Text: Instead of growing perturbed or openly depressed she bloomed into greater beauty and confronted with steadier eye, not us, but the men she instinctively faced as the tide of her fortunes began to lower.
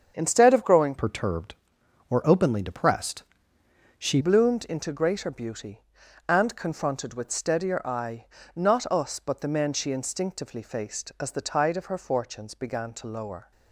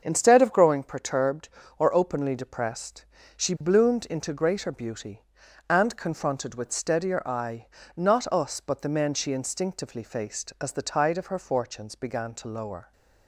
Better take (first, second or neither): second